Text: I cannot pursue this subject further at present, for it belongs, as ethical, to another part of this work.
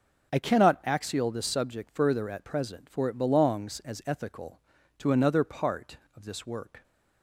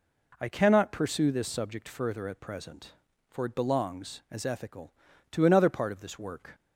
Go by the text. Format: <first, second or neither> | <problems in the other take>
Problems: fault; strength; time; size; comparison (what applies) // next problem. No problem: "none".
second | says "axial" for "pursue"; at 0.8 s